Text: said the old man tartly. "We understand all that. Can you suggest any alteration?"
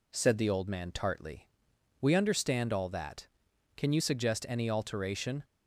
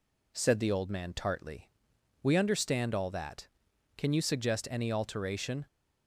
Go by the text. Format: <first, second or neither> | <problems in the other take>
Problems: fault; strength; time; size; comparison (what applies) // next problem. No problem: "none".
neither | none